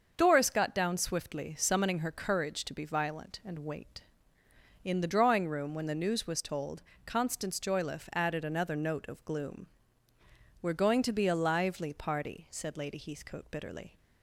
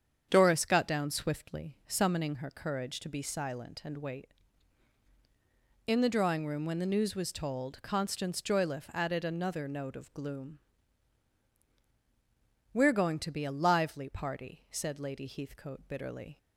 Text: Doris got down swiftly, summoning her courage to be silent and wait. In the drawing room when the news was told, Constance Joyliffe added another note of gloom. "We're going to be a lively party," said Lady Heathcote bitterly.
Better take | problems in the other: second | starts louder than the rest; until 1.1 s; 6.5 dB; strong in the second // says "violent" for "silent"; at 2.8 s

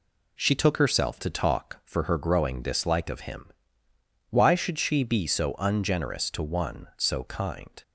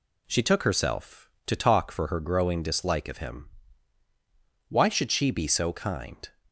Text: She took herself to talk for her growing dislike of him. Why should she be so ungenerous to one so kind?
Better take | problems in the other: first | skips "ungenerous to one so"; at 5.7 s

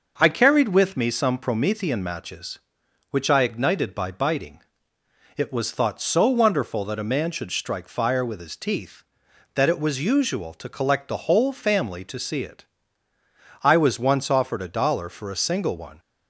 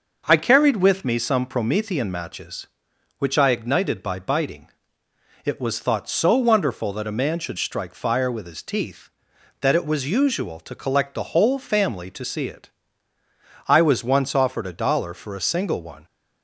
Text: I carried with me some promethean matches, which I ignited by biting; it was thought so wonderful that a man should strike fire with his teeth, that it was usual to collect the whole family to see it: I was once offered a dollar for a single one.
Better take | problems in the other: neither | none

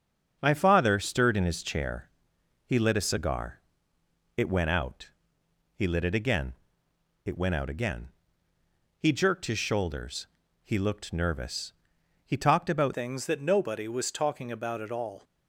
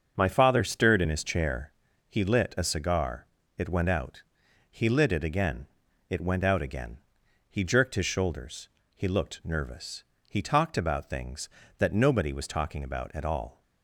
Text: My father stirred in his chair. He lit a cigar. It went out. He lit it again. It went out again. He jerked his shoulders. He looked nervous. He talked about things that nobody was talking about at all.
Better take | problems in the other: second | starts louder than the rest; until 1.4 s; 7 dB; also in the second // changes voice at "things"; from 12.9 s on; 2.3 s long

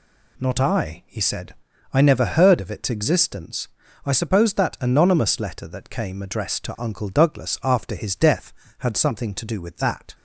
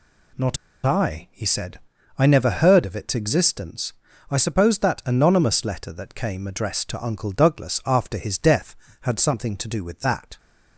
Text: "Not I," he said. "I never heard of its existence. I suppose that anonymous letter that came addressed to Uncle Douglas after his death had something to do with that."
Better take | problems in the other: first | pauses between "Not" and "I"; slight; at 0.5 s; 0.28 s long

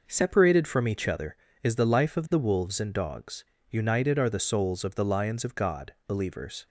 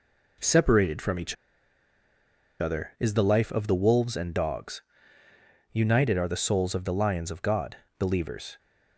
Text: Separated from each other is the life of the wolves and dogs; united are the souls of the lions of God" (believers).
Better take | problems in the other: first | pauses between "each" and "other"; strong; at 1.3 s; 1.2 s long

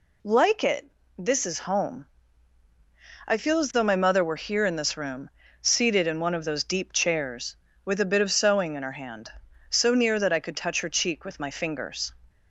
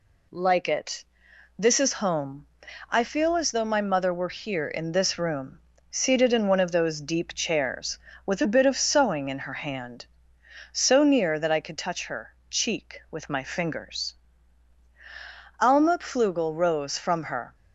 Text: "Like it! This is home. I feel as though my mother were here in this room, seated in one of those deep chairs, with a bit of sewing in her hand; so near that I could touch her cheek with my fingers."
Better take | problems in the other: first | pauses between "her" and "cheek"; slight; at 12.3 s; 0.16 s long // goes on to say "Alma Pflugel rose from her"; strong; from 15.6 s on; 1.9 s long

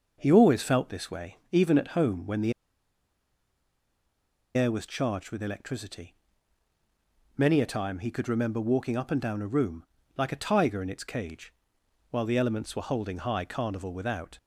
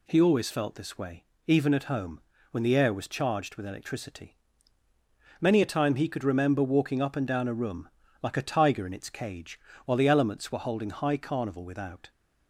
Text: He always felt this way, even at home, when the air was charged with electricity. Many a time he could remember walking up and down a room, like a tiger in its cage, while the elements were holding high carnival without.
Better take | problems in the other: second | pauses between "the" and "air"; strong; at 2.5 s; 2.0 s long

